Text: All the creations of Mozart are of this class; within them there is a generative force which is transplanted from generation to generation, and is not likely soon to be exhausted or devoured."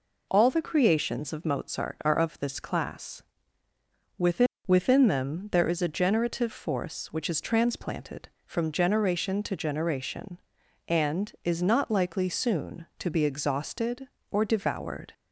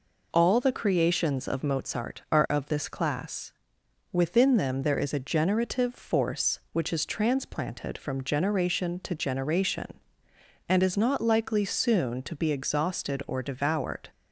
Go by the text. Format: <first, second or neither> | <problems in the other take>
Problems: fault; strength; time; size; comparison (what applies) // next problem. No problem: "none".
second | says "within" twice; at 4.6 s